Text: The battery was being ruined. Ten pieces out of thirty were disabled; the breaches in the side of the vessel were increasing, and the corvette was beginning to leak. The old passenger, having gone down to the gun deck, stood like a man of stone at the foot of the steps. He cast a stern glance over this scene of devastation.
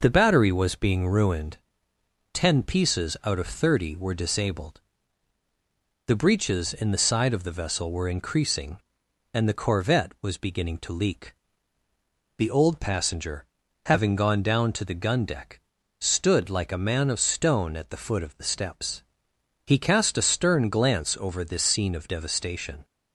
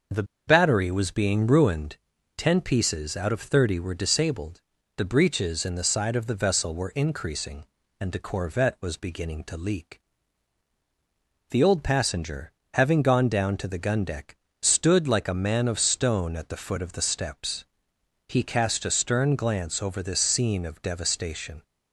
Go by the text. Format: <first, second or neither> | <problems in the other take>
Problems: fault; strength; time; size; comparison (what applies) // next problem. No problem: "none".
first | starts louder than the rest; until 1.3 s; 6.5 dB // pauses between "The" and "battery"; slight; at 0.2 s; 0.23 s long